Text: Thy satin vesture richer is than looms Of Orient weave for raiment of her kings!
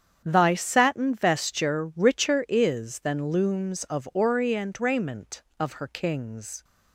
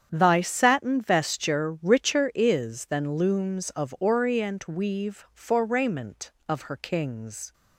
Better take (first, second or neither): second